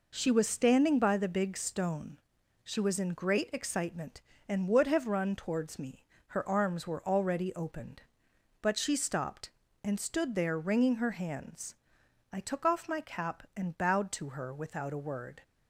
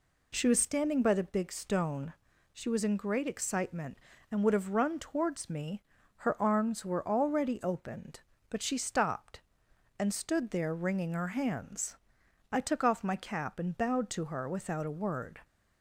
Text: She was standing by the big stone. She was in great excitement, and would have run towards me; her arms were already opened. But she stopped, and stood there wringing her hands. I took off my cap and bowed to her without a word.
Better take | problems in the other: neither | none

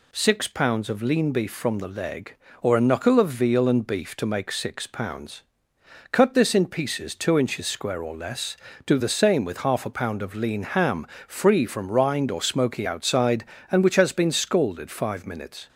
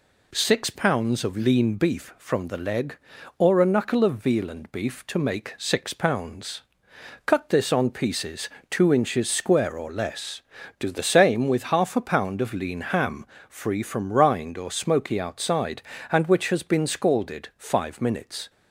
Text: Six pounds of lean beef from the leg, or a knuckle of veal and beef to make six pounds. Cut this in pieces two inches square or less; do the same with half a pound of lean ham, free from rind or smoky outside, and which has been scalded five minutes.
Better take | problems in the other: first | says "on" for "in"; at 7.7 s // pauses between "pieces" and "two"; slight; at 8.4 s; 0.20 s long

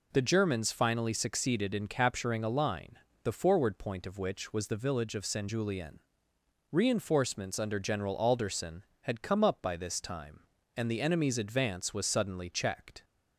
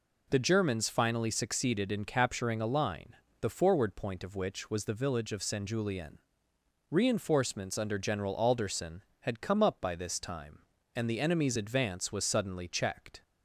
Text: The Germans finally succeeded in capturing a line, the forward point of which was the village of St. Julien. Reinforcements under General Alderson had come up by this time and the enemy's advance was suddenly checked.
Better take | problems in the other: neither | none

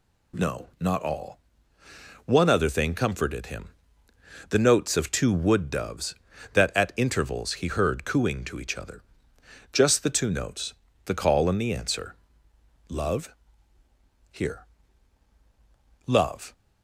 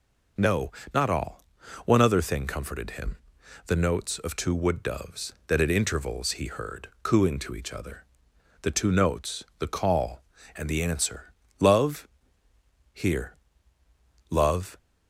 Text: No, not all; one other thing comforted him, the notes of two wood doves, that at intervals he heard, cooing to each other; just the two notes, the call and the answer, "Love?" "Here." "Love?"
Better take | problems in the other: first | skips "just"; at 8.3 s

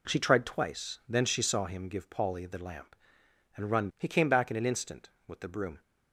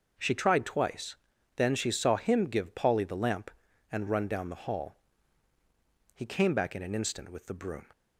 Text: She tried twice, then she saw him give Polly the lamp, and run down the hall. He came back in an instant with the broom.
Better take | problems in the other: second | skips "down the hall"; at 3.9 s

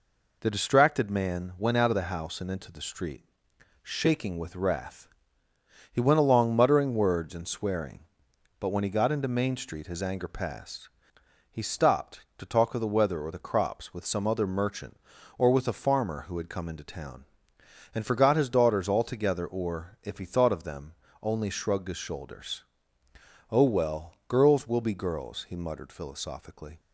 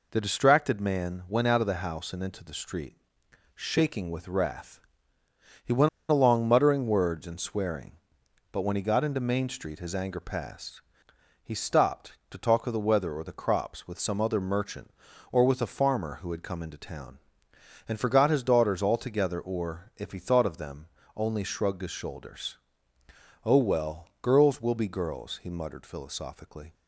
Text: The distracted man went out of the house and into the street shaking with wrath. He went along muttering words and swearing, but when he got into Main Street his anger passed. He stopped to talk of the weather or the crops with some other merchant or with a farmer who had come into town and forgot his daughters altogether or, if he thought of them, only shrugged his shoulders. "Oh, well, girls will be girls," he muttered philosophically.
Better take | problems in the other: first | pauses between "street" and "shaking"; noticeable; at 2.9 s; 0.64 s long; noticeable in the first // pauses between "went" and "along"; slight; at 5.8 s; 0.20 s long

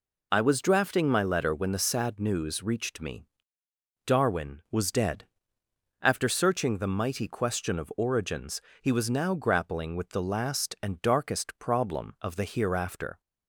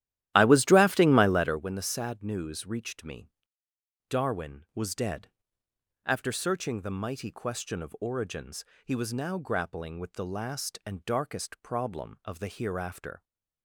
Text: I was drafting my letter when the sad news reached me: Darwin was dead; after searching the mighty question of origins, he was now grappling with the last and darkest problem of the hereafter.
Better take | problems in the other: first | starts louder than the rest; strong; until 1.6 s; 13 dB

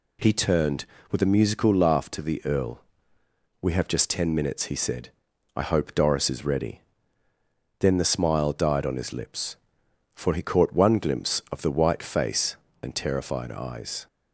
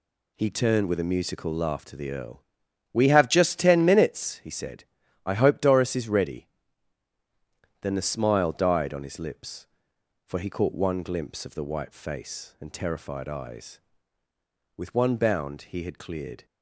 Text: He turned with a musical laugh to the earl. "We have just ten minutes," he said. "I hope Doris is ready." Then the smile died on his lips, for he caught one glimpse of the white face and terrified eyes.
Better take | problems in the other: first | goes on to say "With one bound he had cleared"; strong; from 14.7 s on; 1.7 s long

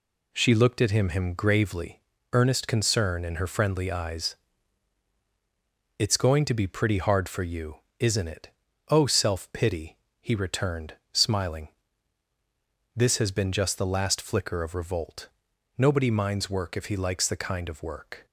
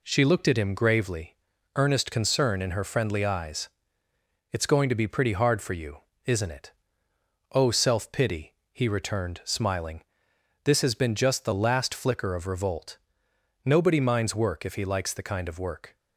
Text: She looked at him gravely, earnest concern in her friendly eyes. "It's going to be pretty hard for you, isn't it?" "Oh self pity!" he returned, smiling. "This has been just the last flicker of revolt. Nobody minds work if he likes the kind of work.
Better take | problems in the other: second | says "him" twice; at 1.0 s

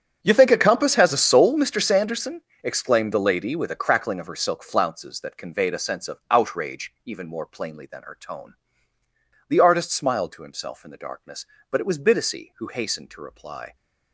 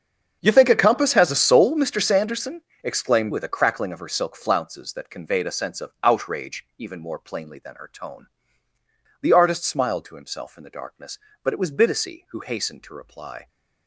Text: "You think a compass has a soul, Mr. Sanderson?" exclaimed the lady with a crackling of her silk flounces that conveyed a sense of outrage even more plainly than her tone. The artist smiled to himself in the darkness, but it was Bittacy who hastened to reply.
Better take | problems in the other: first | starts louder than the rest; strong; until 1.4 s; 7.5 dB; strong in the first // skips "the lady"; at 3.3 s

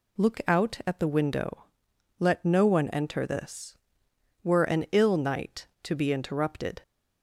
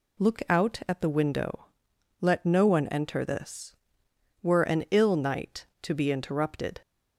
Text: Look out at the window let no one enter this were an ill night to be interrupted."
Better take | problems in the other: neither | pauses between "window" and "let"; noticeable; the same in both

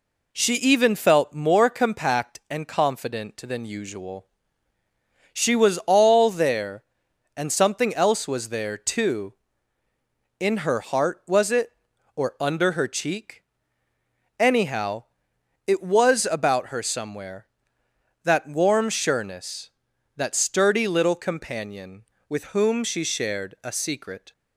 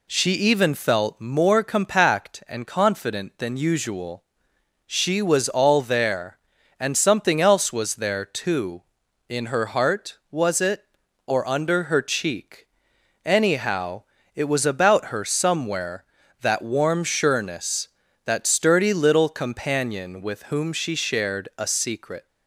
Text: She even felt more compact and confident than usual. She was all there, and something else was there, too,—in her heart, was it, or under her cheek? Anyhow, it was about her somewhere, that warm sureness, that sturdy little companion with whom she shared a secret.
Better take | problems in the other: neither | none

